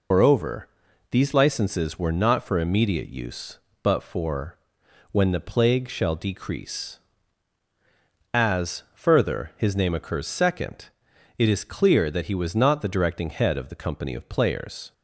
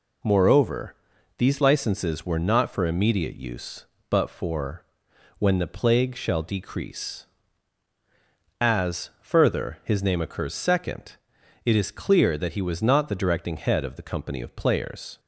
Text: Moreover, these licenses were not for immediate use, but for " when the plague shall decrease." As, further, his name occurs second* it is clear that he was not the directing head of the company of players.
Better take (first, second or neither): second